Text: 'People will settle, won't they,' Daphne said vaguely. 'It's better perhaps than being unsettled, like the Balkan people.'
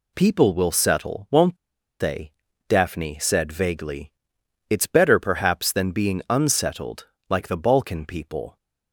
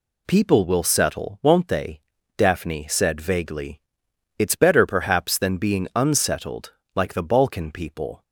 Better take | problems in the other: second | pauses between "won't" and "they"; at 1.5 s; 0.44 s long

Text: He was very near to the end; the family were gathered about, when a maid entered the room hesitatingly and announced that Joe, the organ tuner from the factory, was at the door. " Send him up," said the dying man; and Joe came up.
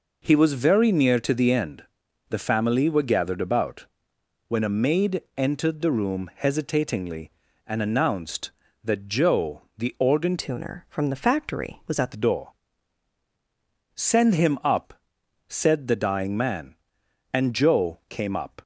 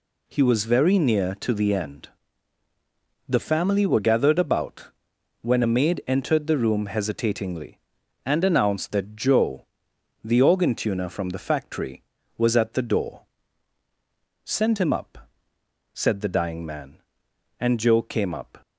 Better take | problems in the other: second | changes voice from "tuner" to "at"; from 10.3 to 12.1 s; 1.8 s long

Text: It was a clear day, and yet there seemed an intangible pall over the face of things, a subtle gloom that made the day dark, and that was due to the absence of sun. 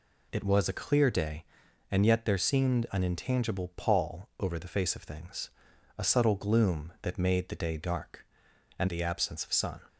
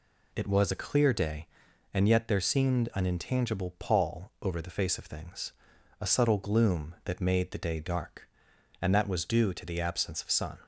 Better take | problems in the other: second | skips "that was due to"; at 8.8 s

